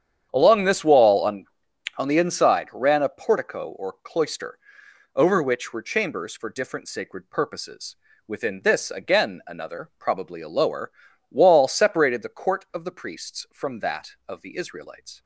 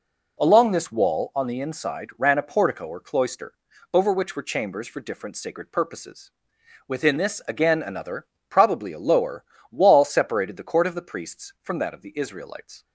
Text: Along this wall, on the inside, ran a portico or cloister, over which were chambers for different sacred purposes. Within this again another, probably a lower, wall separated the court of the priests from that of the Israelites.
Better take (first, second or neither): second